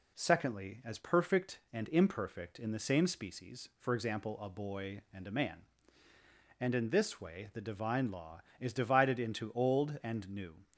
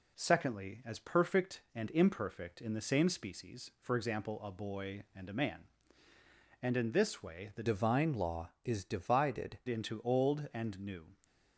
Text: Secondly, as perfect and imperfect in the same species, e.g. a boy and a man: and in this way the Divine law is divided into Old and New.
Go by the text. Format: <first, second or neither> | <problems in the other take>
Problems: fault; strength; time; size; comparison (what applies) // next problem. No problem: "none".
first | changes voice from "Divine" to "divided"; from 7.6 to 9.5 s; 1.9 s long